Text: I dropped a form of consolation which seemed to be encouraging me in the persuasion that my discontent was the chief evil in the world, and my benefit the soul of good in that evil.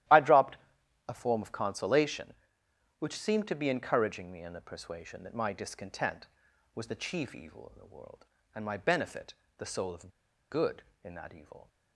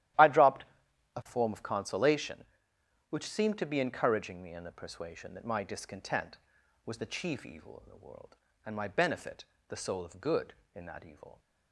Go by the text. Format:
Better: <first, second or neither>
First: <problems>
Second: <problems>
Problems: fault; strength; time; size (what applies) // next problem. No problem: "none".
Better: second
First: starts louder than the rest; strong; until 1.6 s; 13 dB // pauses between "dropped" and "a"; noticeable; at 0.5 s; 0.52 s long // pauses between "benefit" and "the"; slight; at 9.3 s; 0.24 s long // pauses between "of" and "good"; at 10.0 s; 0.42 s long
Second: starts louder than the rest; strong; until 1.7 s; 13 dB // pauses between "dropped" and "a"; noticeable; at 0.6 s; 0.52 s long // pauses between "benefit" and "the"; slight; at 9.4 s; 0.24 s long